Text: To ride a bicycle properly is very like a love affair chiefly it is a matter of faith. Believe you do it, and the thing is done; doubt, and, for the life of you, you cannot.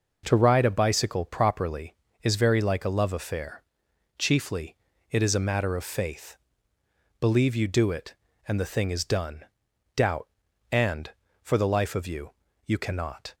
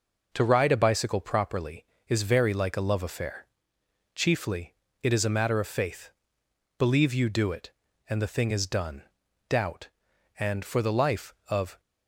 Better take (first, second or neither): first